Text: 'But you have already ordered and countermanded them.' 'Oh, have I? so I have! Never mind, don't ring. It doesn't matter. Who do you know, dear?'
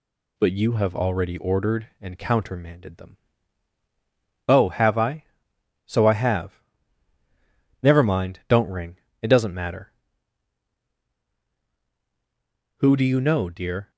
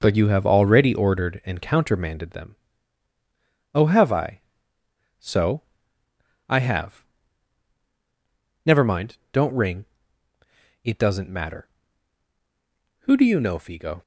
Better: first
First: none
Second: pauses between "so" and "I"; noticeable; at 5.6 s; 0.86 s long // says "figo" for "dear"; at 13.5 s

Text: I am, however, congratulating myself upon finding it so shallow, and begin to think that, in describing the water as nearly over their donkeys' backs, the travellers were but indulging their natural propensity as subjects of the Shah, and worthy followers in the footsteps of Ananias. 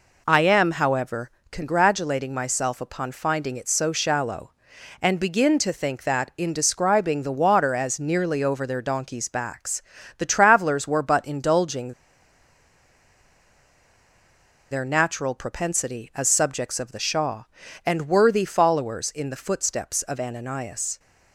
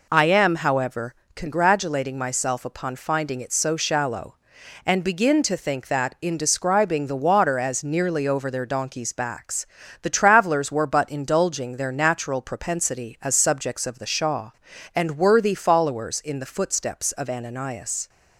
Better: second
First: pauses between "indulging" and "their"; strong; at 11.9 s; 2.7 s long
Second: none

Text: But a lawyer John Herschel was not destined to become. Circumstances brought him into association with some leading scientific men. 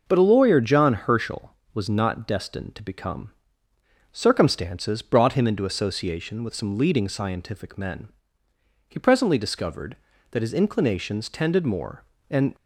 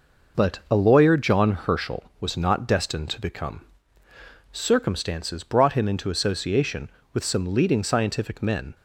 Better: second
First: goes on to say "He presently discovered that his inclinations tended more and"; strong; from 8.8 s on; 3.6 s long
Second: none

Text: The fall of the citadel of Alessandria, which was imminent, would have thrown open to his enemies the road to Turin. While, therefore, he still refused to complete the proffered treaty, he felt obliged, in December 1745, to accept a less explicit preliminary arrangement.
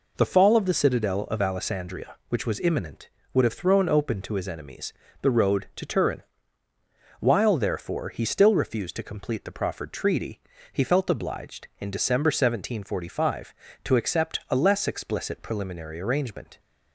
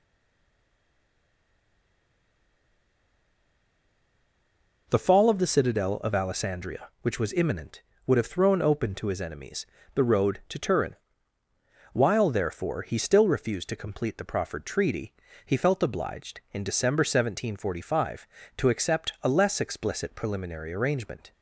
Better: first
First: pauses between "enemies" and "the"; slight; at 4.9 s; 0.30 s long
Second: stays silent before the first word; strong; until 4.8 s; 4.8 s long // pauses between "enemies" and "the"; slight; at 9.6 s; 0.30 s long

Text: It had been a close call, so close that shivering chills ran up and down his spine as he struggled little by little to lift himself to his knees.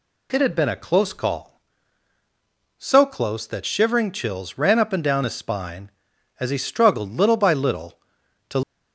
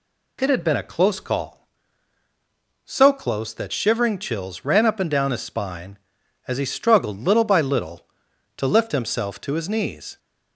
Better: second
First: stops before "lift himself to his knees"; at 8.6 s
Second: none

